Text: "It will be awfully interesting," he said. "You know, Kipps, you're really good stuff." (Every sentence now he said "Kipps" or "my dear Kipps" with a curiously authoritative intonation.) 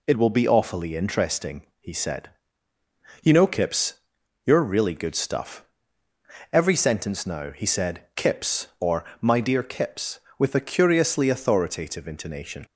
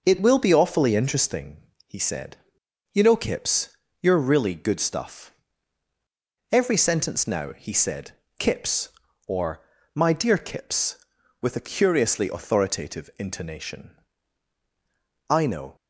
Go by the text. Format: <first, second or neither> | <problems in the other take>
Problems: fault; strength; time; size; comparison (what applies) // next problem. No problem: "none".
first | pauses between "said" and "Kipps"; slight; at 8.1 s; 0.24 s long; slight in the first // pauses between "or" and "my"; slight; at 9.6 s; 0.32 s long; slight in the first // goes on to say "I know"; slight; from 15.2 s on; 0.46 s long